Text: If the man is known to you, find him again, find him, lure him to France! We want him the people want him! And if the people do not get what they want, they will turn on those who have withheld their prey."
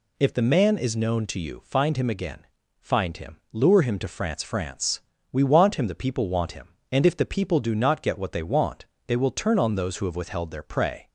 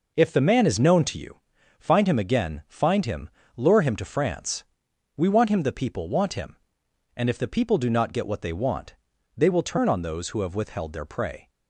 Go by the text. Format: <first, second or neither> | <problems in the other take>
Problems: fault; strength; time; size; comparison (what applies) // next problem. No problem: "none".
second | says "France" twice; at 4.4 s